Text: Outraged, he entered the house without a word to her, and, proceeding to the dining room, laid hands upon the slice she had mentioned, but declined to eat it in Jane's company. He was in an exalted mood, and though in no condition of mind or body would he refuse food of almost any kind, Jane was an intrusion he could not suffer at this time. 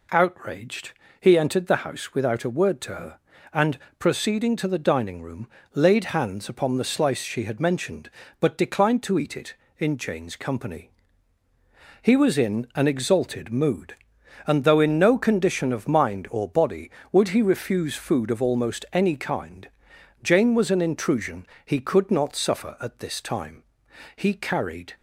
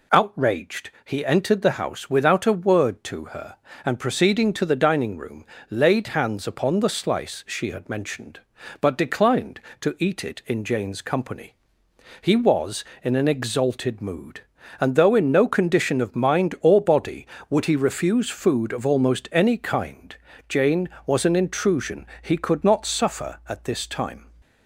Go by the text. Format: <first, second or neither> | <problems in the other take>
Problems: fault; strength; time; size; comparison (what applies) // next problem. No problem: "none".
second | pauses between "intrusion" and "he"; slight; at 21.4 s; 0.18 s long; slight in the second // goes on to say "He carried"; noticeable; from 24.1 s on; 0.78 s long